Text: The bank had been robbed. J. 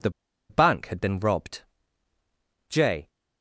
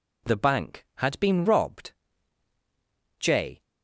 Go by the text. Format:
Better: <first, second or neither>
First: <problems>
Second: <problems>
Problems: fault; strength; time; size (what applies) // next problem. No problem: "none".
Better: second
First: pauses between "The" and "bank"; at 0.0 s; 0.40 s long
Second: none